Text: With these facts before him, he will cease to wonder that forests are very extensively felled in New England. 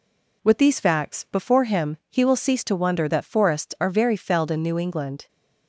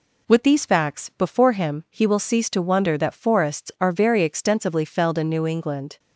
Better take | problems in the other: second | skips "extensively"; at 4.1 s

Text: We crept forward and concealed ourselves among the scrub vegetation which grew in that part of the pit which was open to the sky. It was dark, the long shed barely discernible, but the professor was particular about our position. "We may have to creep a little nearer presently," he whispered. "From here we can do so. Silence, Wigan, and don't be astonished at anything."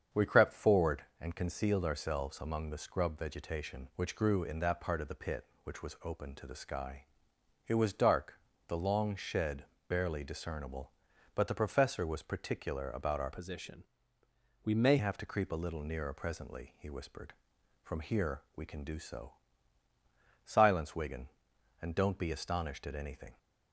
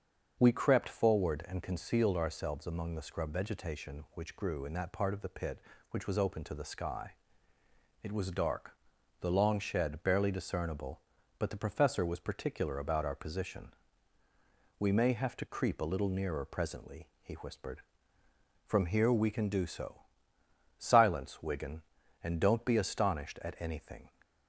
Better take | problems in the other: second | starts louder than the rest; strong; until 1.3 s; 7.5 dB; also in the second // pauses between "shed" and "barely"; slight; at 9.6 s; 0.24 s long // changes voice from "position" to "may"; from 13.3 to 14.9 s; 1.6 s long

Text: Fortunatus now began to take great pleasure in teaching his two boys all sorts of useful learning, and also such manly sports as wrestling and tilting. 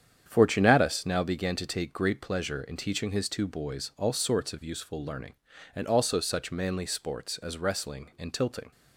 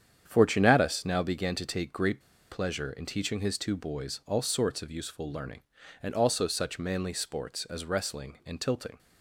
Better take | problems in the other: first | starts louder than the rest; strong; until 1.2 s; 8.5 dB; strong in the first // pauses between "great" and "pleasure"; slight; at 2.2 s; 0.30 s long

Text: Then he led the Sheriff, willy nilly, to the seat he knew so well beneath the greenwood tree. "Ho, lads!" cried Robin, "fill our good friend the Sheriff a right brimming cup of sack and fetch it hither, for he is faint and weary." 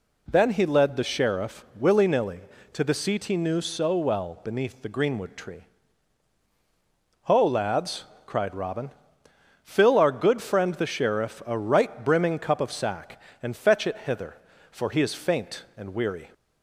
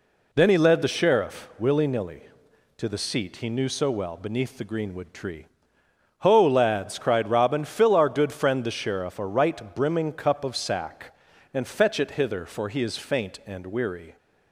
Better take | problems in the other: neither | none

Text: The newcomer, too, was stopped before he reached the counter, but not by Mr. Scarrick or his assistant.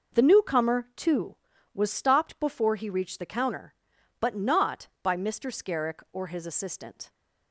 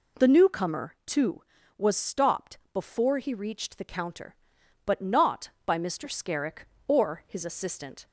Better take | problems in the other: neither | none

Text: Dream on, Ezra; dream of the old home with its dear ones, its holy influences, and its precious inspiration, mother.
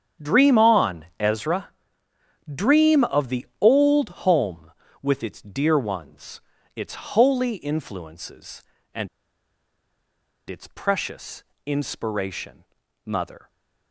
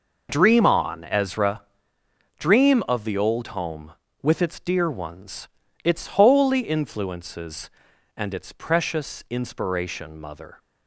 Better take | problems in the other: second | starts louder than the rest; strong; until 1.3 s; 8 dB // pauses between "and" and "its"; strong; at 9.0 s; 1.4 s long // pauses between "precious" and "inspiration"; slight; at 11.4 s; 0.20 s long

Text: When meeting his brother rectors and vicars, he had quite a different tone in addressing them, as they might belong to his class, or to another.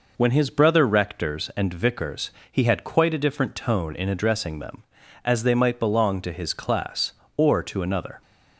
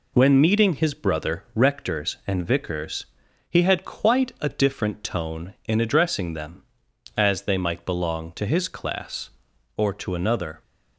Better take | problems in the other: second | skips "meeting"; at 0.3 s

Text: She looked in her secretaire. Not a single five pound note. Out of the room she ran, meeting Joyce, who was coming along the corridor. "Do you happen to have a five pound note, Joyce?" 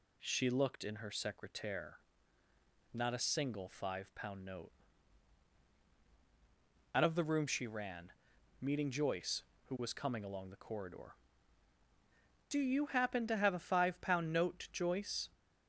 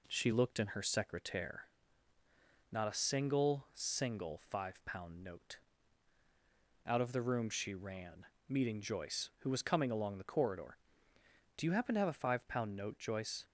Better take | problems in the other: first | says "single" twice; at 3.7 s

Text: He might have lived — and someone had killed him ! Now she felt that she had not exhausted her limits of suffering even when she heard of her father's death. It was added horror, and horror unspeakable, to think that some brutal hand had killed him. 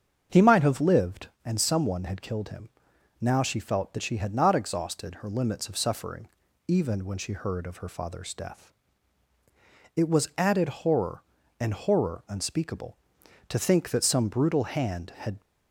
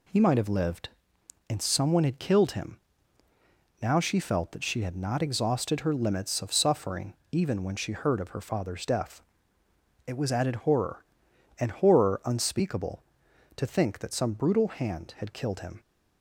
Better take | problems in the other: second | starts louder than the rest; strong; until 1.4 s; 7.5 dB // pauses between "suffering" and "even"; at 6.2 s; 0.38 s long; slight in the second // stops before "killed him"; at 15.4 s

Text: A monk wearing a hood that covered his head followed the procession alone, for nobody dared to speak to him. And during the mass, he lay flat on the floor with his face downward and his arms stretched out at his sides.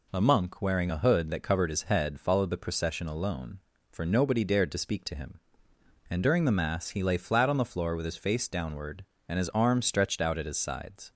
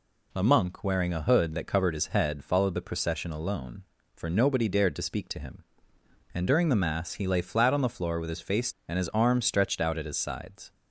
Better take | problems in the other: first | skips "downward"; at 8.7 s

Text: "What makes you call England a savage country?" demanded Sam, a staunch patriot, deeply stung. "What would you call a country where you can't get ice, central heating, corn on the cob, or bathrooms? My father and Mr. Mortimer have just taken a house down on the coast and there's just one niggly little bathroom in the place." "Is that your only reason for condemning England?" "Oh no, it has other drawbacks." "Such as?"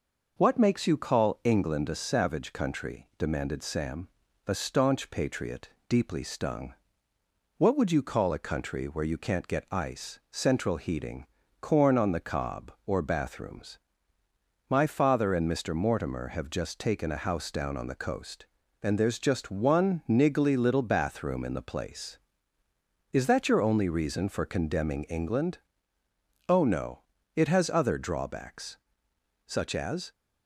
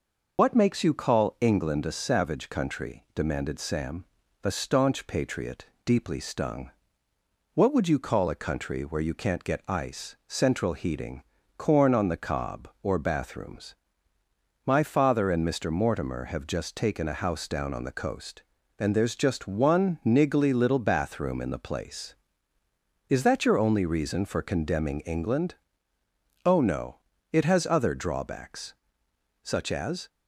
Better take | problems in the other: first | loses the start of "What"; at 0.3 s; 50 ms

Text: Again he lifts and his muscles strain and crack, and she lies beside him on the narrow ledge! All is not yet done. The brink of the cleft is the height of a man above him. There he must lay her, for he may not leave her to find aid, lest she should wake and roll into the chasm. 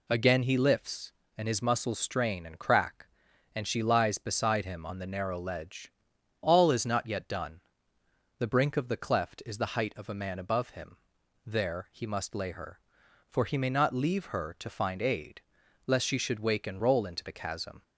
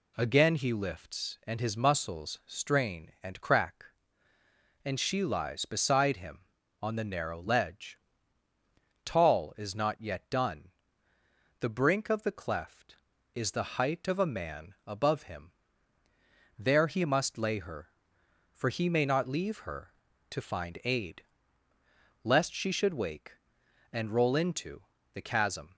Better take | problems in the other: first | says "Tall" for "All"; at 9.0 s // pauses between "into" and "the"; slight; at 24.8 s; 0.30 s long

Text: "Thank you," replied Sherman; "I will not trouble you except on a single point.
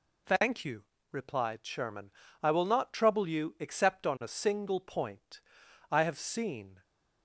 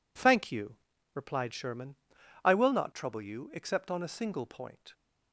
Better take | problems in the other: second | goes on to say "I have seen"; noticeable; from 5.9 s on; 0.92 s long

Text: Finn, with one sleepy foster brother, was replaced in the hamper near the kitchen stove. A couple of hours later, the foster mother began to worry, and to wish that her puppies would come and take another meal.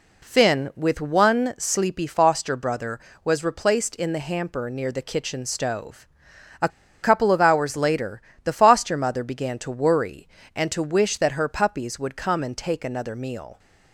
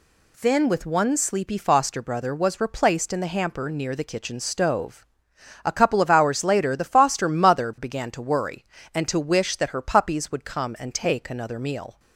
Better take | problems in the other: second | pauses between "A" and "couple"; slight; at 6.6 s; 0.33 s long

